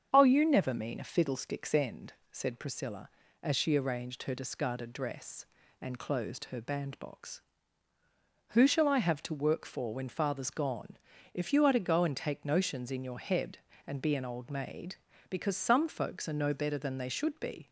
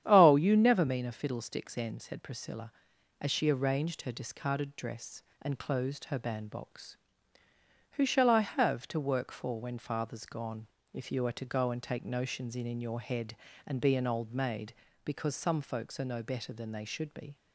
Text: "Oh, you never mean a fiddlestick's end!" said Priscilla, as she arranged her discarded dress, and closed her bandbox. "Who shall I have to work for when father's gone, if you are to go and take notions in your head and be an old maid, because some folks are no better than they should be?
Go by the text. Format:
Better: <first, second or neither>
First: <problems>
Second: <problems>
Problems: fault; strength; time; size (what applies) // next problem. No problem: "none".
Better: first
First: starts louder than the rest; strong; until 1.1 s; 7.5 dB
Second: starts louder than the rest; strong; until 1.0 s; 10 dB // says "in" twice; at 12.6 s